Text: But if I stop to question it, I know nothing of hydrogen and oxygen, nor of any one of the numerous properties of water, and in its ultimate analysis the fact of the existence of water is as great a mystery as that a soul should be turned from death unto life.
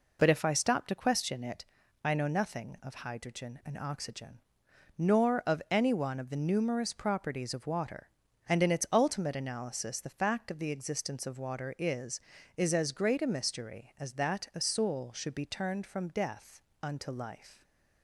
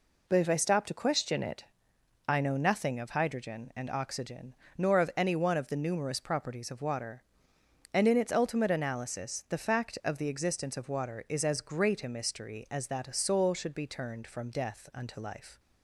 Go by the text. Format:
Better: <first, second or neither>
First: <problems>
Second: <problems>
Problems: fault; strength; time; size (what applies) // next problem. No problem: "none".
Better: second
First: says "is" twice; at 12.5 s // pauses between "death" and "unto"; slight; at 16.6 s; 0.22 s long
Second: none